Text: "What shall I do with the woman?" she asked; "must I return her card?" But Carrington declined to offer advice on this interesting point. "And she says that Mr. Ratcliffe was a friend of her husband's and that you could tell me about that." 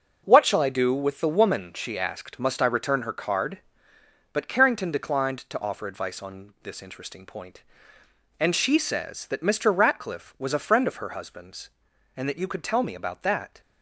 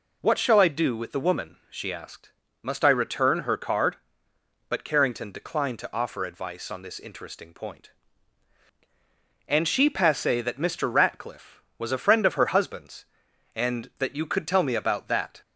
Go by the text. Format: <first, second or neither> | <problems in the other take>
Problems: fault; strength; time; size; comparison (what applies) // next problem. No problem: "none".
first | says "passe" for "says"; at 9.8 s